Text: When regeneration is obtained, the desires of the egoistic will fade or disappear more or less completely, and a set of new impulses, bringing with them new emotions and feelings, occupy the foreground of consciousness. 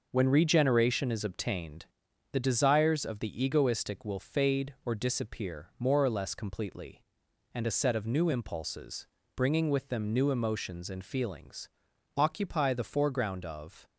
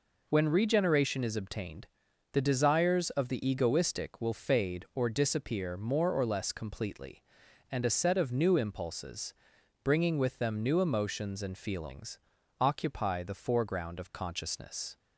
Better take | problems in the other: second | stops before "consciousness"; at 13.8 s

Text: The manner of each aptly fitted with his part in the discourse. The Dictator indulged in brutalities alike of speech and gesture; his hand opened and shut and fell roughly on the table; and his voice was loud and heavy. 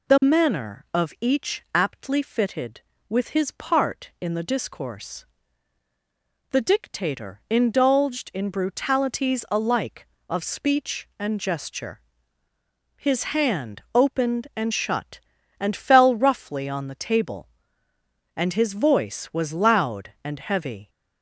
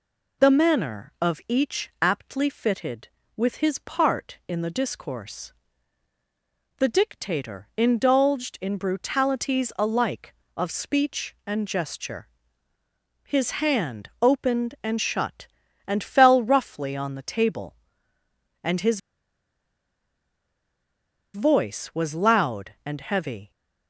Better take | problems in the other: first | pauses between "his" and "voice"; strong; at 18.9 s; 2.3 s long

